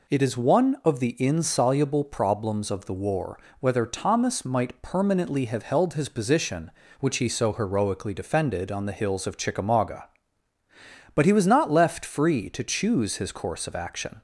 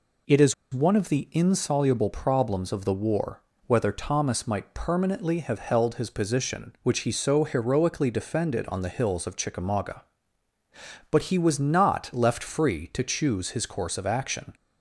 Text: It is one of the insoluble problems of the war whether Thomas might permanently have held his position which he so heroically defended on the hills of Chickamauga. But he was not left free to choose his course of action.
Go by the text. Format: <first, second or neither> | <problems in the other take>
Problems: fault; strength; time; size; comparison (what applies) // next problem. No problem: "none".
first | pauses between "is" and "one"; slight; at 0.5 s; 0.20 s long // pauses between "war" and "whether"; slight; at 3.4 s; 0.26 s long; slight in the first